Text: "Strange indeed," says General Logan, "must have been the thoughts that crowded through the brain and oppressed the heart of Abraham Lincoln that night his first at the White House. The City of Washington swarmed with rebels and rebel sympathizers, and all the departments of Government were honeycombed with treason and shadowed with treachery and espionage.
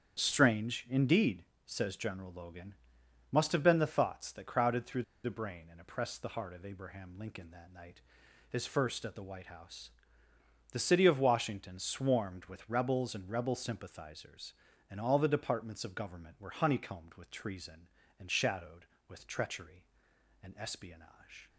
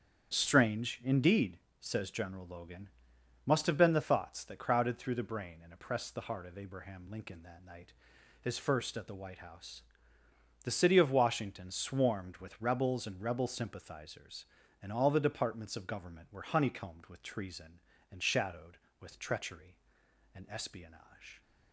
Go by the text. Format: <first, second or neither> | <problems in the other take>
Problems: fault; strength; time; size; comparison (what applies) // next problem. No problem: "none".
second | starts louder than the rest; strong; until 1.2 s; 8.5 dB; strong in the second // pauses between "through" and "the"; slight; at 5.0 s; 0.20 s long // pauses between "night" and "his"; noticeable; at 8.0 s; 0.46 s long; noticeable in the second